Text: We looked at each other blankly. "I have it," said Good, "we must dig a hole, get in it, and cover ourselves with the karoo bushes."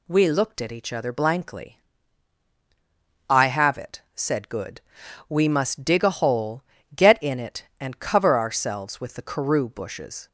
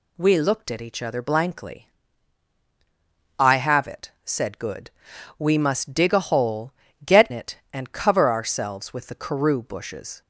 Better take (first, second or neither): first